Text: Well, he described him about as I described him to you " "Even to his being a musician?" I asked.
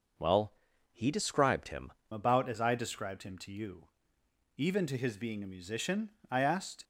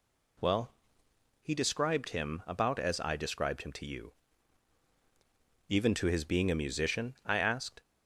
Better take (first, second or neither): second